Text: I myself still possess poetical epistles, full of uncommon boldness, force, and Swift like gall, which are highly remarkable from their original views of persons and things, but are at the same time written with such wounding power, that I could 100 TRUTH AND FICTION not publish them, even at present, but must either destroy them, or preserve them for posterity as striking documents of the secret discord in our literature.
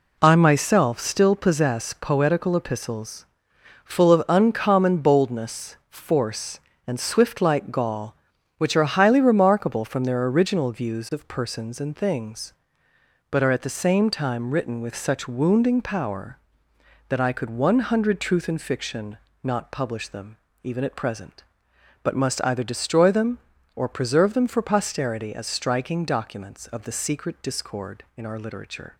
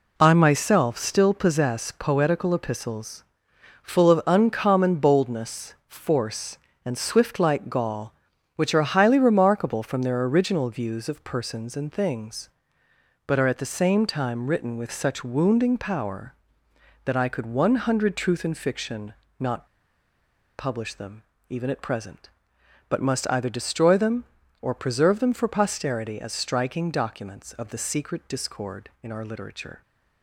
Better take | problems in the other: first | pauses between "FICTION" and "not"; slight; at 19.1 s; 0.26 s long; slight in the first // pauses between "not" and "publish"; noticeable; at 19.6 s; 0.89 s long

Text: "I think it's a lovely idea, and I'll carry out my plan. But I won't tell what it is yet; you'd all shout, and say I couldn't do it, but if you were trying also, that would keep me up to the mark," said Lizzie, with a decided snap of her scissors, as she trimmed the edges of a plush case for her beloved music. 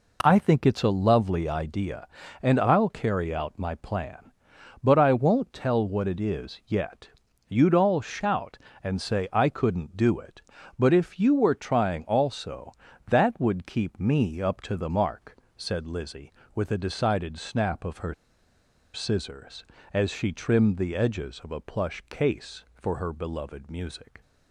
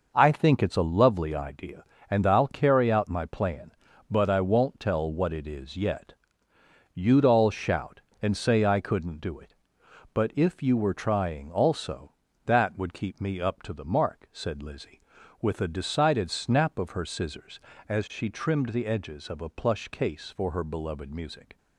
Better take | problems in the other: second | pauses between "her" and "scissors"; noticeable; at 18.1 s; 0.80 s long

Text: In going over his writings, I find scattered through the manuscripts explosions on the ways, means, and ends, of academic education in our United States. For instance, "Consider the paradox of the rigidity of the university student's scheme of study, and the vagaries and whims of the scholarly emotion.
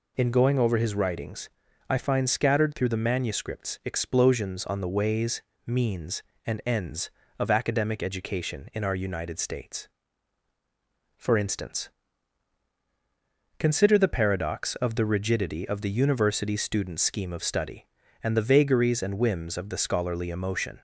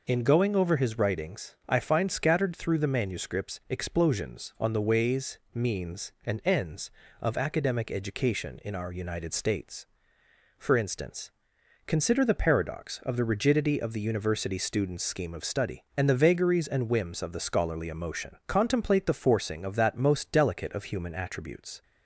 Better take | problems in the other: first | goes on to say "Contemplate the forcing of that most delicate of human attributes"; strong; from 18.4 s on; 3.3 s long

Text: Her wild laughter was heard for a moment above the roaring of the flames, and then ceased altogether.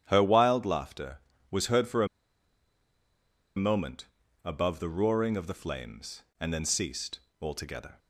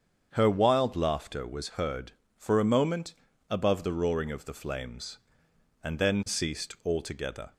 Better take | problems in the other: second | starts louder than the rest; strong; until 1.0 s; 10.5 dB; strong in the second // pauses between "a" and "moment"; strong; at 2.0 s; 1.4 s long // pauses between "moment" and "above"; at 4.0 s; 0.38 s long; slight in the second // pauses between "ceased" and "altogether"; slight; at 7.2 s; 0.20 s long

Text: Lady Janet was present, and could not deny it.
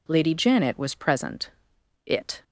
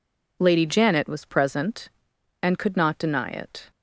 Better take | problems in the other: second | skips "and could not deny"; at 1.7 s

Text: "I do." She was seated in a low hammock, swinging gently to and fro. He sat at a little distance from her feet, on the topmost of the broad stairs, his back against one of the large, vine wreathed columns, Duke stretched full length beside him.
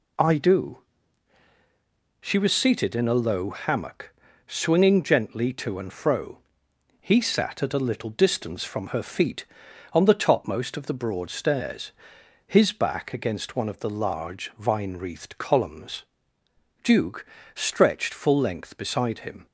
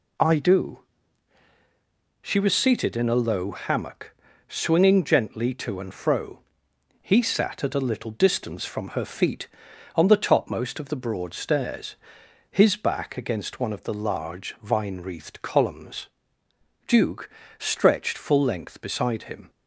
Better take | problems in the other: neither | pauses between "Duke" and "stretched"; slight; the same in both

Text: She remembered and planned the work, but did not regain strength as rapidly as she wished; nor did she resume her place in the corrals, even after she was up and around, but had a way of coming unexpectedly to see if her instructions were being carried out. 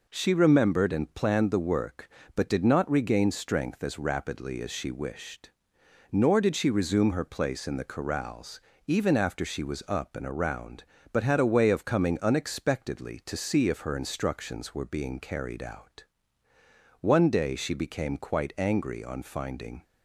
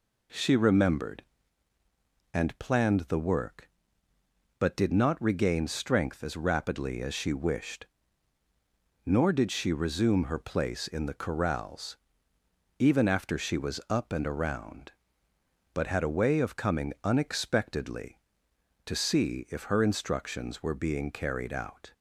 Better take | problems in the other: second | goes on to say "One day she became quite angry on finding"; strong; from 17.0 s on; 2.8 s long

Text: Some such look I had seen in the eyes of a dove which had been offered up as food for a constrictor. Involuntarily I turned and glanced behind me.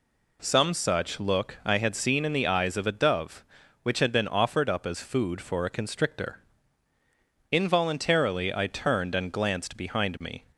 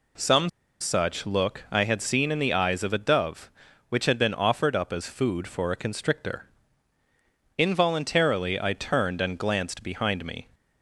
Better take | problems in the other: first | pauses between "Some" and "such"; slight; at 0.4 s; 0.32 s long

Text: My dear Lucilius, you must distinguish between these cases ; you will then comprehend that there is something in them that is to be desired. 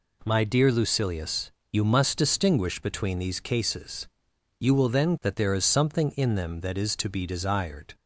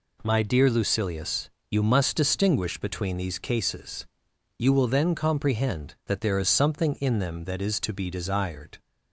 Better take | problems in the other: second | skips "comprehend"; at 5.1 s

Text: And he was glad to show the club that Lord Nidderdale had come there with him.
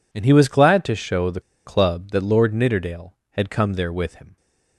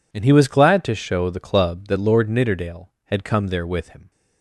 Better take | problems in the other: second | pauses between "the" and "club"; slight; at 1.3 s; 0.25 s long

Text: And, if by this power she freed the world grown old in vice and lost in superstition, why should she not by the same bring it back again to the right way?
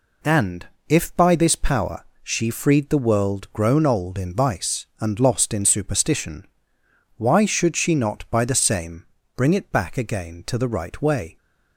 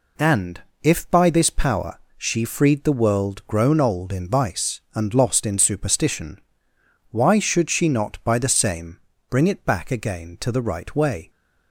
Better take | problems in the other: neither | pauses between "power" and "she"; slight; the same in both // pauses between "same" and "bring"; slight; the same in both

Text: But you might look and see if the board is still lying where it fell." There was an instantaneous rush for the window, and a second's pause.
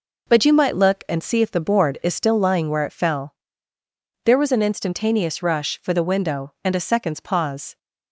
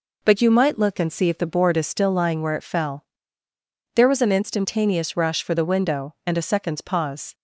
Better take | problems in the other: neither | none

